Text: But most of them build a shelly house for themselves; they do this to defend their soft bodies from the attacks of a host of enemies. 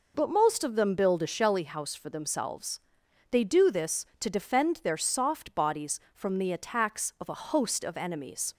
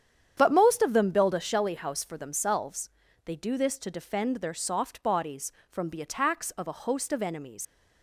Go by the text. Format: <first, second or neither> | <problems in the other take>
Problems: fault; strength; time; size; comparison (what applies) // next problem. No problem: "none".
first | starts louder than the rest; strong; until 1.3 s; 9 dB // leaves "enemies" unfinished; at 7.6 s; 90 ms